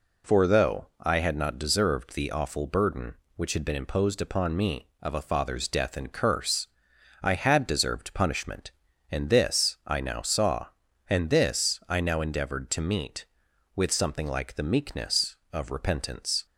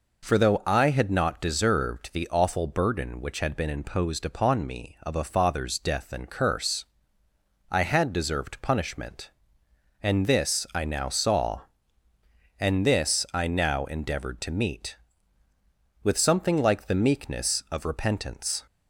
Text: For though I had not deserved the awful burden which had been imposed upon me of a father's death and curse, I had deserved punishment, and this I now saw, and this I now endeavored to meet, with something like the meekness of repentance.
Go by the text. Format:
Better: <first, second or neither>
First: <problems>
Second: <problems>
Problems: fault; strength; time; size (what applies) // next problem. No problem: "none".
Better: neither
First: none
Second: none